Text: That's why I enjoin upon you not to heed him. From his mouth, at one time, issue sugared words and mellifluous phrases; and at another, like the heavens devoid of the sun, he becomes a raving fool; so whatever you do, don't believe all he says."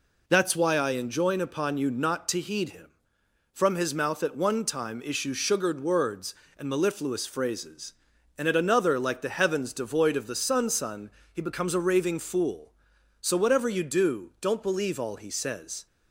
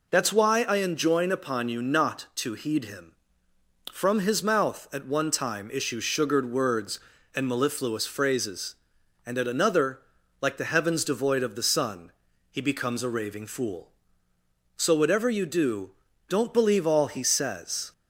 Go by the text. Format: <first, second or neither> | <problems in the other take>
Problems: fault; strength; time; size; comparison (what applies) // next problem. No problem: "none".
second | says "sun" twice; at 10.6 s